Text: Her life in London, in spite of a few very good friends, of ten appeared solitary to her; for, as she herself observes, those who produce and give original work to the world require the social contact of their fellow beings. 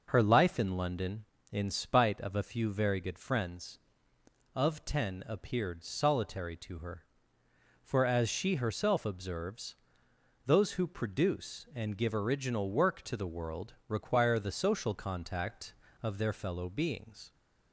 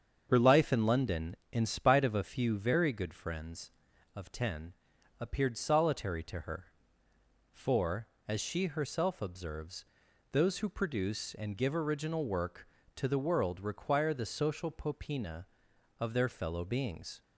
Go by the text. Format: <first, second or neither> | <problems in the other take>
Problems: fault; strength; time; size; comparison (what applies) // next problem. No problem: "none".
first | starts louder than the rest; strong; until 1.3 s; 7 dB // pauses between "ten" and "appeared"; noticeable; at 4.7 s; 0.46 s long // says "popina" for "contact"; at 14.6 s